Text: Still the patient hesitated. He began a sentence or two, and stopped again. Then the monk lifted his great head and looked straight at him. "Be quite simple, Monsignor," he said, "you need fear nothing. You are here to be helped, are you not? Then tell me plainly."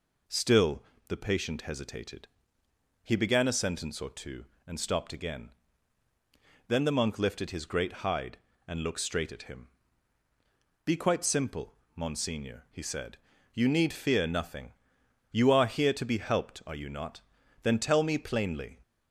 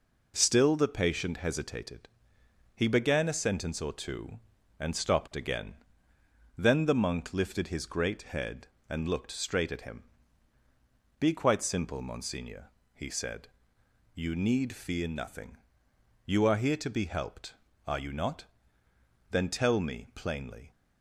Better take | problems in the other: second | pauses between "Still" and "the"; slight; at 0.8 s; 0.26 s long // says "hide" for "head"; at 8.0 s

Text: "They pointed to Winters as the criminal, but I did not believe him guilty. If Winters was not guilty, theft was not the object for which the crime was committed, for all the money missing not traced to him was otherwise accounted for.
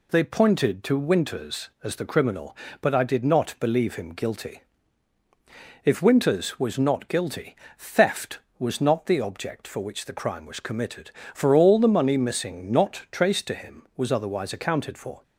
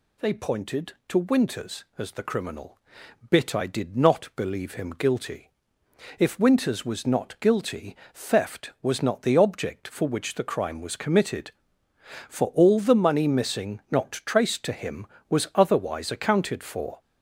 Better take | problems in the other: first | says "bit" for "but"; at 3.2 s

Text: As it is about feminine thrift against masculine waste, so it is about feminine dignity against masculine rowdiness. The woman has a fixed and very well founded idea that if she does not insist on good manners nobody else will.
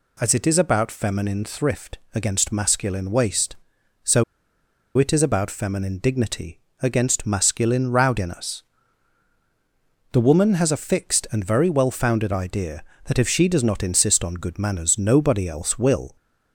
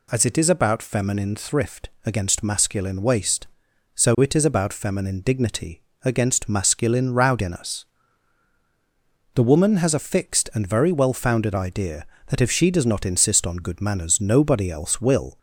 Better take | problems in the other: second | pauses between "so" and "it"; noticeable; at 4.2 s; 0.73 s long // pauses between "dignity" and "against"; slight; at 6.5 s; 0.22 s long; slight in the second

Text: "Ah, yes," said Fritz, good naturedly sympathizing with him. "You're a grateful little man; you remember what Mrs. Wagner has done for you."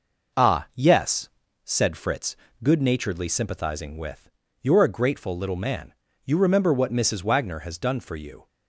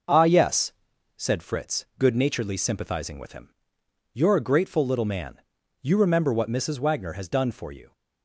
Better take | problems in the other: second | skips "him"; at 4.4 s

